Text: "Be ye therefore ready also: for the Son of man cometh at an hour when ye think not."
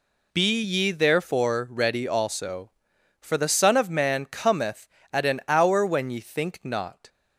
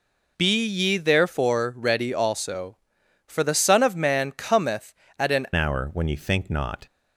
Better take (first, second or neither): first